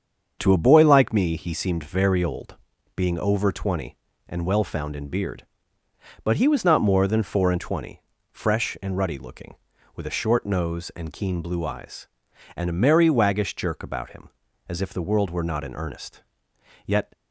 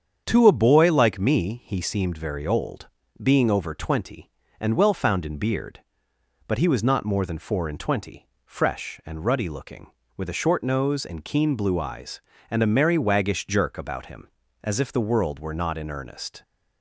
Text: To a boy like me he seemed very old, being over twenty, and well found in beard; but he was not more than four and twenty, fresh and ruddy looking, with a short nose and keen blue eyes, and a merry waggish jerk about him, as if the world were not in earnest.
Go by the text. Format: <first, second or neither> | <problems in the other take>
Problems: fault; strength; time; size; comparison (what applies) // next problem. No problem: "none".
second | starts louder than the rest; until 1.4 s; 7 dB; strong in the second // goes on to say "Yet"; slight; from 16.8 s on; 0.26 s long